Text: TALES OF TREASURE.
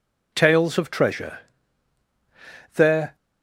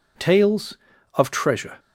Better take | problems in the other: second | goes on to say "There"; slight; from 2.7 s on; 0.40 s long

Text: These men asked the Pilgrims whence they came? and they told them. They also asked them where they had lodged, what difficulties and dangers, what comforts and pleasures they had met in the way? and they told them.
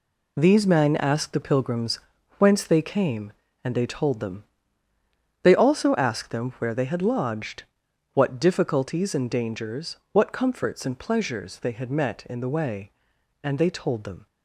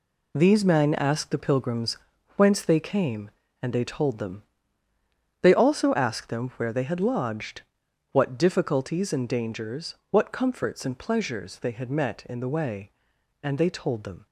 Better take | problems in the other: neither | pauses between "Pilgrims" and "whence"; the same in both

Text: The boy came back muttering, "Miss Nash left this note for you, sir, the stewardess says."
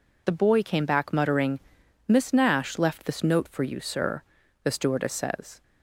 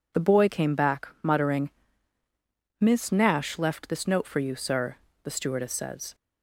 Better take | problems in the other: neither | none

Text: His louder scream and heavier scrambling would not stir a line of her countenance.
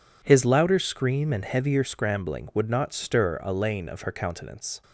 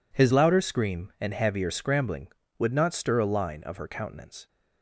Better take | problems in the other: second | says "lane" for "line"; at 3.5 s

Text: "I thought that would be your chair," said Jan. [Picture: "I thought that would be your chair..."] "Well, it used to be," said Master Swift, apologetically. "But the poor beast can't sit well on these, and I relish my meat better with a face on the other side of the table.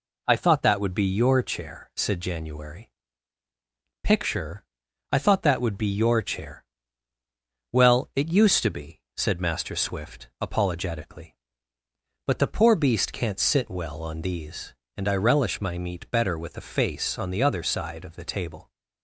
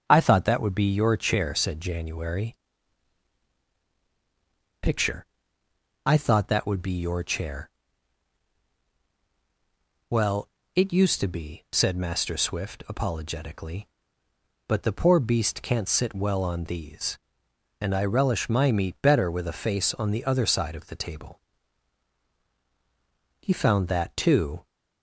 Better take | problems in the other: first | starts louder than the rest; strong; until 1.0 s; 7.5 dB // goes on to say "He found that too"; noticeable; from 23.3 s on; 1.2 s long

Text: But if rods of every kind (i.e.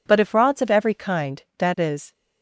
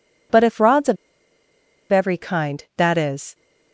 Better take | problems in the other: first | pauses between "of" and "every"; noticeable; at 0.9 s; 0.94 s long

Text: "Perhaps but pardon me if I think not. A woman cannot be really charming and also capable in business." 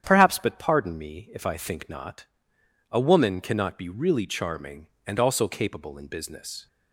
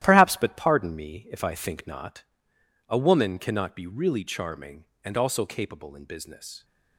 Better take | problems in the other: first | gets quieter; strong; throughout; 10 dB // starts louder than the rest; strong; until 1.0 s; 13 dB; strong in the first

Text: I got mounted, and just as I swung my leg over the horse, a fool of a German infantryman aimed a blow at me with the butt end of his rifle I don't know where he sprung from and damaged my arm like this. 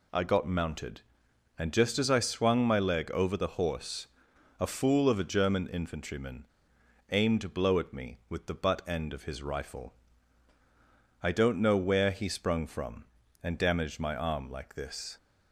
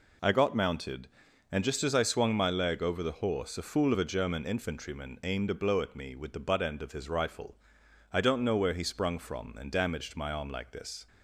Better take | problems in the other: second | pauses between "infantryman" and "aimed"; noticeable; at 6.4 s; 0.63 s long // pauses between "rifle" and "I"; strong; at 9.9 s; 1.2 s long; noticeable in the second

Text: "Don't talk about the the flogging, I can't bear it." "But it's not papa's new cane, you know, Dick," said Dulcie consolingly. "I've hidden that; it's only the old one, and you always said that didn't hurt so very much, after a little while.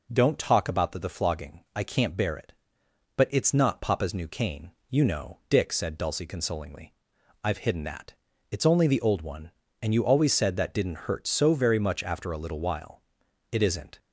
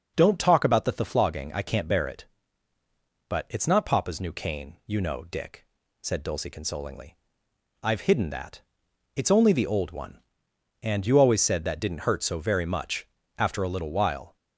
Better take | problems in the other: second | goes on to say "It isn't"; slight; from 13.5 s on; 0.48 s long

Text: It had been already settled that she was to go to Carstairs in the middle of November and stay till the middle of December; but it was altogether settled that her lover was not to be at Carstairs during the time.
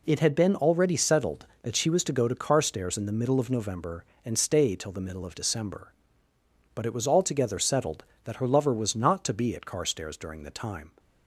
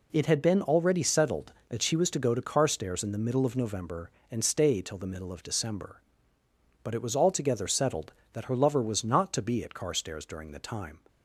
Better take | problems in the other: neither | none

